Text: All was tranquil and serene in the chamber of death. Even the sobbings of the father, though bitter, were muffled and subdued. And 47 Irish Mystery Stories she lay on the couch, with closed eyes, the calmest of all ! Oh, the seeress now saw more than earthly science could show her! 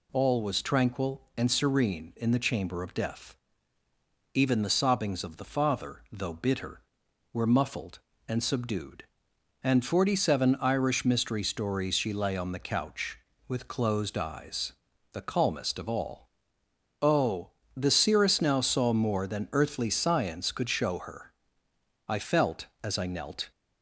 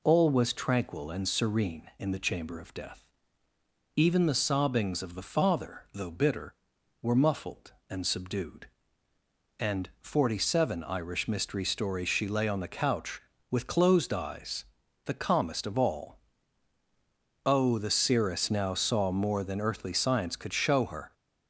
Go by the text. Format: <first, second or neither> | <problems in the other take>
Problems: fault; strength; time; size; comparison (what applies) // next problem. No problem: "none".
second | goes on to say "I felt as I knelt"; from 22.0 s on; 1.4 s long